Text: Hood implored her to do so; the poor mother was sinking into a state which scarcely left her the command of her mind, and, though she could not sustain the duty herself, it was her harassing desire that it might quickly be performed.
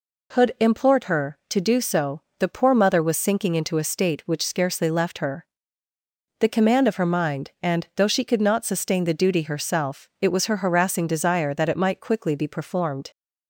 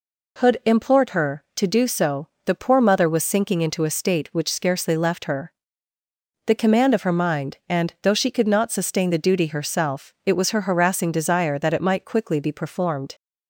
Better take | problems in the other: neither | pauses between "her" and "the"; noticeable; the same in both

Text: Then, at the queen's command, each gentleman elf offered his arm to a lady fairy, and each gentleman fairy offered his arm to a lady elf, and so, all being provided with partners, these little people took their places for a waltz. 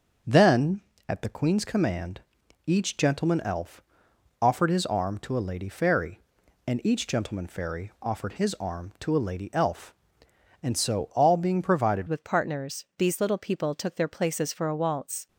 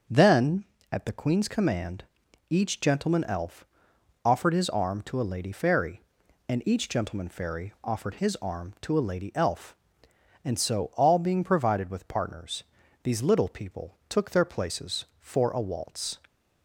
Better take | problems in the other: second | starts louder than the rest; until 1.5 s; 6 dB; also in the second // pauses between "elf" and "offered"; noticeable; at 3.8 s; 0.58 s long; noticeable in the second // changes voice at "with"; from 12.0 s on; 3.2 s long

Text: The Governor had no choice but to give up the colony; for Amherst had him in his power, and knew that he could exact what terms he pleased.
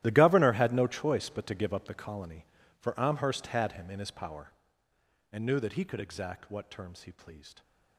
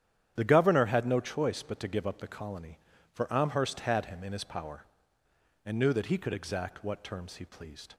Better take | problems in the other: second | gets quieter; strong; throughout; 17.5 dB // starts louder than the rest; strong; until 1.0 s; 13.5 dB; strong in the second

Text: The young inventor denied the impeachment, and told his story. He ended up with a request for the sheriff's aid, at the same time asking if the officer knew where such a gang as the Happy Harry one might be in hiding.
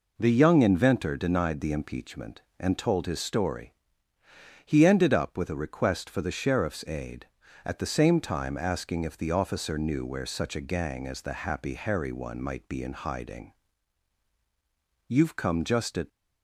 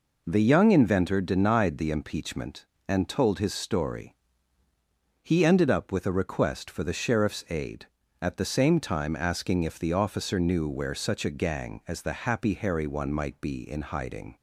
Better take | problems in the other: second | goes on to say "You've come just at"; noticeable; from 15.0 s on; 1.0 s long

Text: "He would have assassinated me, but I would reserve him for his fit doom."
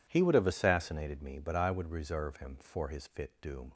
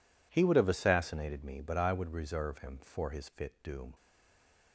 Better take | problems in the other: first | stays silent after the last word; slight; from 3.9 s on; 0.8 s long

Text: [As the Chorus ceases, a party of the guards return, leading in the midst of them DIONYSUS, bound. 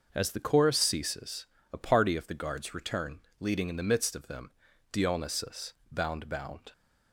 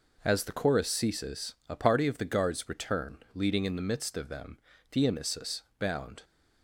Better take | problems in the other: second | starts louder than the rest; noticeable; until 1.1 s; 6 dB // pauses between "them" and "DIONYSUS"; at 4.5 s; 0.40 s long; slight in the second // says "bound" twice; at 6.2 s

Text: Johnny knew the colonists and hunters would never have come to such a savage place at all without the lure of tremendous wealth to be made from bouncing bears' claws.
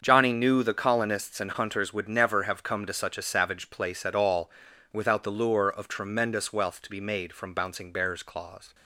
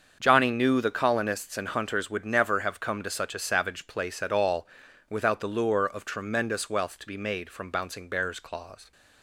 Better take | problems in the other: neither | starts louder than the rest; the same in both // pauses between "all" and "without"; the same in both

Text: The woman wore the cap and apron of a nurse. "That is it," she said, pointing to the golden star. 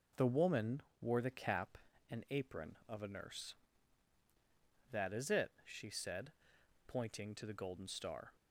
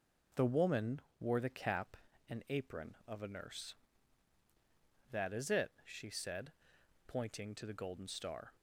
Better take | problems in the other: neither | pauses between "woman" and "wore"; slight; the same in both

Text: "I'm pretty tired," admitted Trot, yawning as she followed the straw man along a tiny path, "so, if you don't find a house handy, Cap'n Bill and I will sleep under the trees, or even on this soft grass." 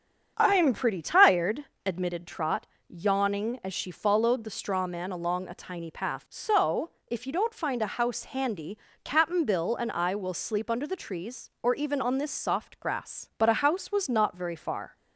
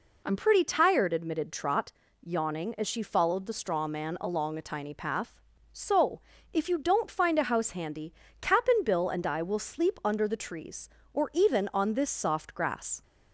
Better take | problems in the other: second | starts louder than the rest; strong; until 1.3 s; 7.5 dB // goes on to say "But a house was not very far"; from 13.3 s on; 1.5 s long

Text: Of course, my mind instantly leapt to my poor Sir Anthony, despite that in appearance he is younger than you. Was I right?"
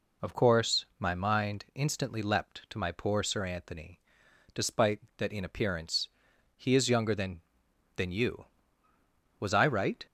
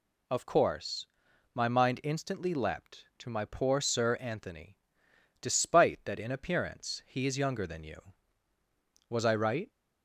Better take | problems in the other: second | pauses between "appearance" and "he"; noticeable; at 6.0 s; 0.50 s long // says "than" twice; at 7.9 s

